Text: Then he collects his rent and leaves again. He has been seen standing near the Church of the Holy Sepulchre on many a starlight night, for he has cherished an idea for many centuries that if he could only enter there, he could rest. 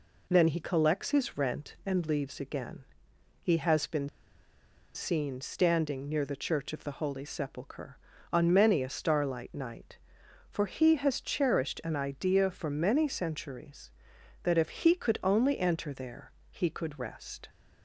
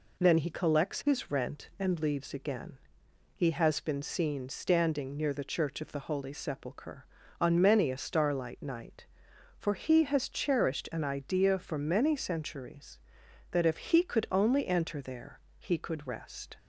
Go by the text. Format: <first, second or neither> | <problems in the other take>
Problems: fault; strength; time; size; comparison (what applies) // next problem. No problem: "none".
second | pauses between "been" and "seen"; noticeable; at 4.0 s; 0.85 s long